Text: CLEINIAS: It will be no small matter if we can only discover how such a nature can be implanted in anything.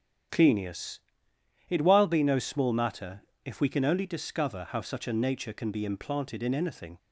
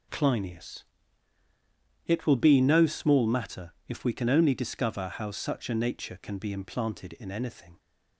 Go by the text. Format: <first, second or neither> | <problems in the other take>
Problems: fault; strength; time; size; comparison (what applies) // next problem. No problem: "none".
second | starts louder than the rest; strong; until 2.0 s; 9.5 dB // says "while" for "will"; at 1.8 s // pauses between "matter" and "if"; slight; at 3.2 s; 0.22 s long